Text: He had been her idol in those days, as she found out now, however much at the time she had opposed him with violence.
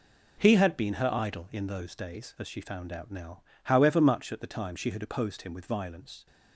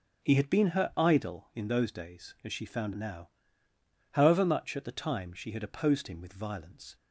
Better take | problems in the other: first | skips "out"; at 2.9 s

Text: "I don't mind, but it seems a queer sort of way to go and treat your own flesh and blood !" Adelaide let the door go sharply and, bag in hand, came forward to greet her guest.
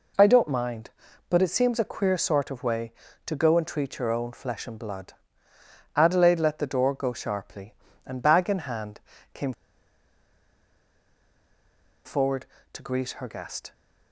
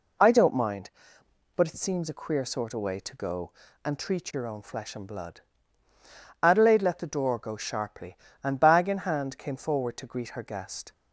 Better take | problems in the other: second | pauses between "came" and "forward"; strong; at 9.5 s; 2.5 s long

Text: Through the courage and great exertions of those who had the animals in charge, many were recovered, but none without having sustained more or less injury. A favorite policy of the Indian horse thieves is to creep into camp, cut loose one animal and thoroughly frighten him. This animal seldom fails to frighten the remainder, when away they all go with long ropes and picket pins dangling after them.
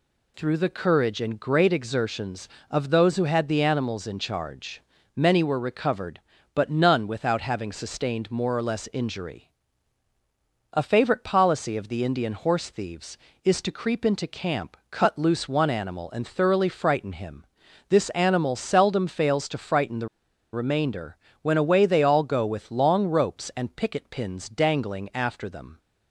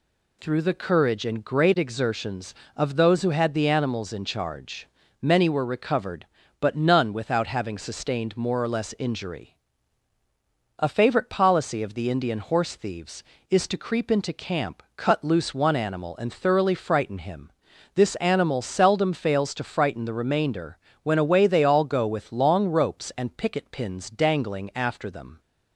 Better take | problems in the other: second | pauses between "the" and "remainder"; at 20.0 s; 0.44 s long

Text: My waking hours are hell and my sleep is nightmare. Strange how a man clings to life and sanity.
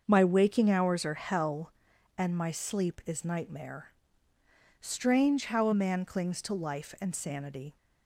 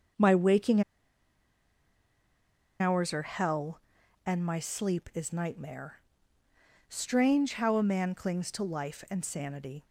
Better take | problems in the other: first | starts louder than the rest; until 3.1 s; 6.5 dB; also in the first // pauses between "waking" and "hours"; strong; at 0.8 s; 1.9 s long

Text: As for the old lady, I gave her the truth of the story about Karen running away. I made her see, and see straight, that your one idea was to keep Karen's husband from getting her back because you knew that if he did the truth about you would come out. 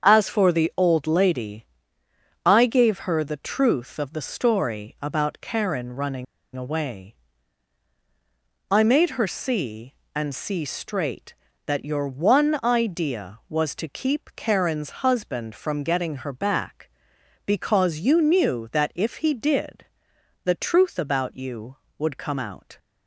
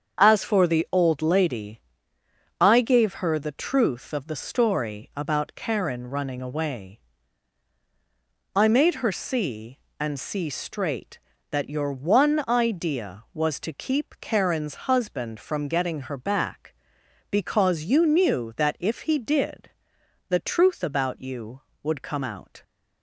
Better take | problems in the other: second | starts louder than the rest; strong; until 1.1 s; 7 dB; strong in the second // pauses between "running" and "away"; slight; at 6.2 s; 0.31 s long // pauses between "did" and "the"; noticeable; at 19.8 s; 0.60 s long; noticeable in the second

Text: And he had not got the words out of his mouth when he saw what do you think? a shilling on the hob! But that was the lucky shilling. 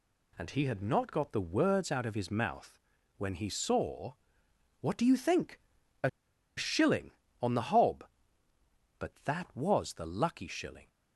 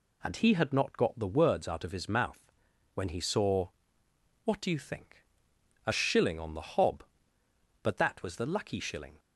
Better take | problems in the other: second | pauses between "mouth" and "when"; at 2.7 s; 0.40 s long; also in the second // pauses between "saw" and "what"; noticeable; at 4.1 s; 0.66 s long; noticeable in the second // pauses between "a" and "shilling"; noticeable; at 6.0 s; 0.47 s long

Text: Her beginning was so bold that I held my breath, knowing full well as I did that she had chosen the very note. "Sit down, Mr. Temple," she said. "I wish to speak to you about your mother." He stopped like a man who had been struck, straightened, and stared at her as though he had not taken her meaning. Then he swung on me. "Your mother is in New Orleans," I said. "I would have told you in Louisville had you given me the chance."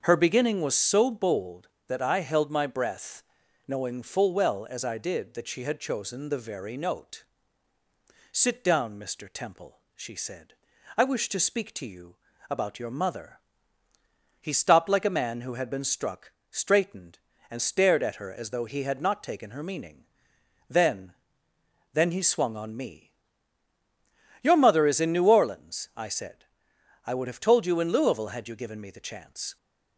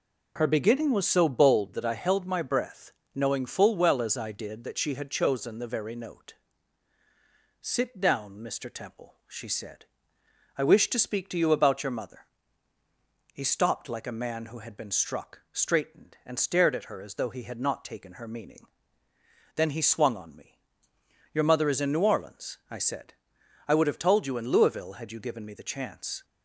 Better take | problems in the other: second | starts louder than the rest; until 1.0 s; 6.5 dB // pauses between "you" and "about"; slight; at 12.1 s; 0.32 s long // says "Then" twice; at 21.9 s

